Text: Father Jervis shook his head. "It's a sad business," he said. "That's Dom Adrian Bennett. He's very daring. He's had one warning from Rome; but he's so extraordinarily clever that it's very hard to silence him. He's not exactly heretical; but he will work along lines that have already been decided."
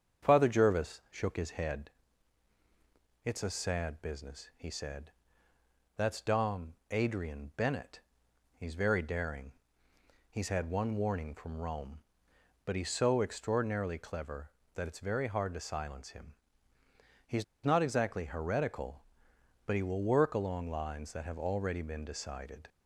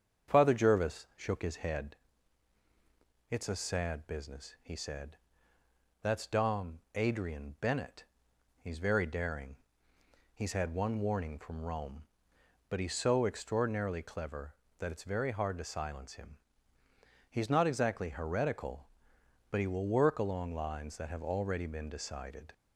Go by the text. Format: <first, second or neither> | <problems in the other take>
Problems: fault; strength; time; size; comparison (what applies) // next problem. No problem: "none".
second | starts louder than the rest; strong; until 1.3 s; 7.5 dB; strong in the second // pauses between "Dom" and "Adrian"; slight; at 6.7 s; 0.16 s long // pauses between "He's" and "not"; slight; at 17.4 s; 0.19 s long